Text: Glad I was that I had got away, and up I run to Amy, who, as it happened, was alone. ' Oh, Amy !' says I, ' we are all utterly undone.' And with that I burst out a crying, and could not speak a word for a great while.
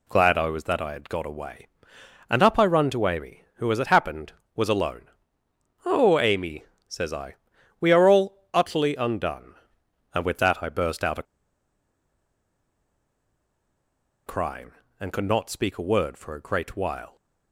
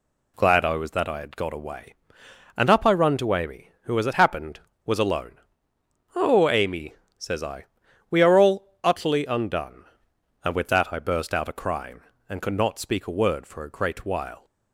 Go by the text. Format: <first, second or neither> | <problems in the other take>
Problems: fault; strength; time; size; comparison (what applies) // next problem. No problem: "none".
second | pauses between "a" and "crying"; strong; at 11.2 s; 3.0 s long